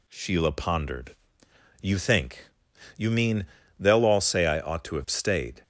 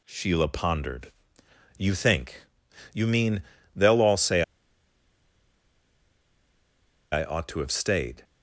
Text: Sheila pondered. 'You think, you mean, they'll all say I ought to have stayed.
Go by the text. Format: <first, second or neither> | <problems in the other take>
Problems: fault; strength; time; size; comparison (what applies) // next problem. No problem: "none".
first | pauses between "say" and "I"; strong; at 4.4 s; 2.7 s long